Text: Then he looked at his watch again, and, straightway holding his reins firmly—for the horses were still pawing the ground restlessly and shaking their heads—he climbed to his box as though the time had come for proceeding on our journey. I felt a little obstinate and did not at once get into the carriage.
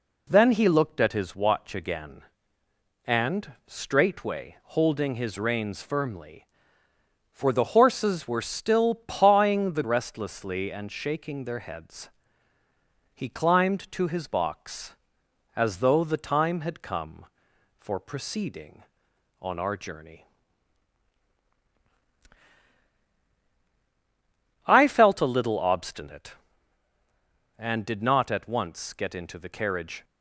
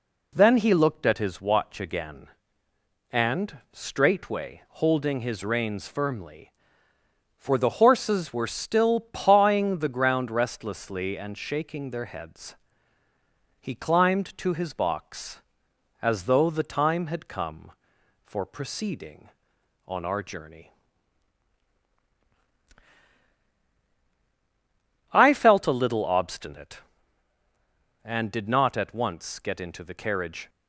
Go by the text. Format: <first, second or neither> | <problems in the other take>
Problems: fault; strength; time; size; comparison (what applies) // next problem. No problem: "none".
second | skips "ground"; at 9.8 s